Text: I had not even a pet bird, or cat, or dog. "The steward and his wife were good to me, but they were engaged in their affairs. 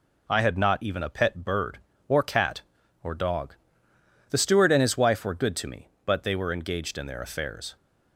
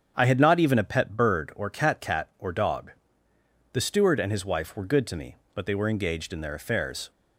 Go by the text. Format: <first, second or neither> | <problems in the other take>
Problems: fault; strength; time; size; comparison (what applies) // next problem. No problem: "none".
first | starts louder than the rest; strong; until 1.1 s; 8 dB // says "cat" twice; at 2.0 s